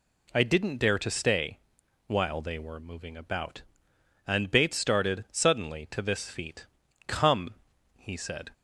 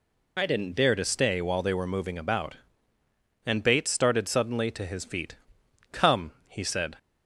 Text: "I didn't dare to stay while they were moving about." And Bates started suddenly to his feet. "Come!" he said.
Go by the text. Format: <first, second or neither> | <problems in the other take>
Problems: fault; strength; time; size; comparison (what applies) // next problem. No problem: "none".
second | pauses between "stay" and "while"; noticeable; at 1.5 s; 0.48 s long // says "this" for "his"; at 6.0 s